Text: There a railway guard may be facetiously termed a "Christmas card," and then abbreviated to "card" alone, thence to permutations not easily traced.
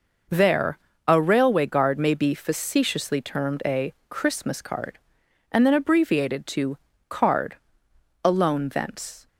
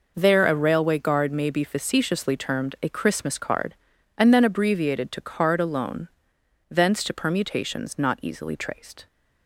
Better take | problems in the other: second | pauses between "There" and "a"; slight; at 0.7 s; 0.30 s long // pauses between "a" and "Christmas"; slight; at 3.9 s; 0.18 s long // pauses between "to" and "card"; slight; at 6.7 s; 0.32 s long // pauses between "card" and "alone"; noticeable; at 7.5 s; 0.66 s long // stops before "to permutations not easily traced"; at 9.2 s

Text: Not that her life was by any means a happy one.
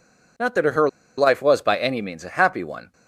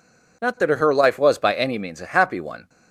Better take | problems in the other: second | pauses between "her" and "life"; slight; at 0.8 s; 0.29 s long

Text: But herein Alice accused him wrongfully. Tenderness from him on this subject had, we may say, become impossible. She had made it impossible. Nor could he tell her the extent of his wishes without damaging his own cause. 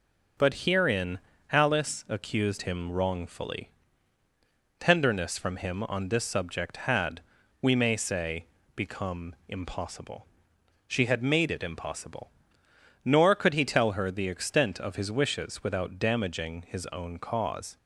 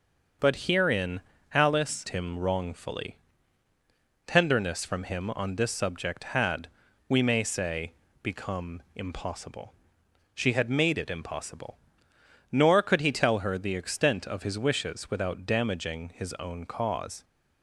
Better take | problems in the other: first | starts louder than the rest; noticeable; until 1.7 s; 6 dB // pauses between "herein" and "Alice"; slight; at 1.2 s; 0.32 s long; slight in the first // skips "accused"; at 2.0 s

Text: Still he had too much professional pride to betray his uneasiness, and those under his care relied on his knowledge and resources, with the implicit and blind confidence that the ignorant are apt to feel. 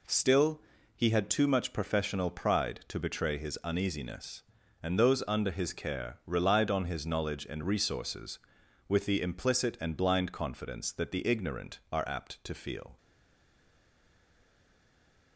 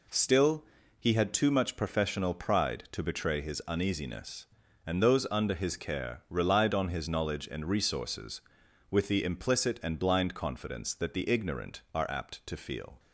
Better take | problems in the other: second | pauses between "Still" and "he"; slight; at 0.6 s; 0.34 s long; slight in the second // stays silent after the last word; from 12.9 s on; 2.4 s long

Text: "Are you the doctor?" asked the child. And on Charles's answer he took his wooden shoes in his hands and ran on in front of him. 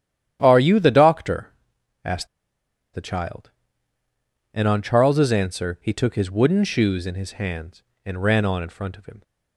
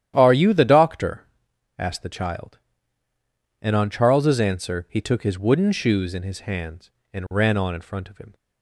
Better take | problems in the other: second | starts louder than the rest; strong; until 1.4 s; 11 dB; strong in the second // pauses between "asked" and "the"; noticeable; at 2.2 s; 0.67 s long

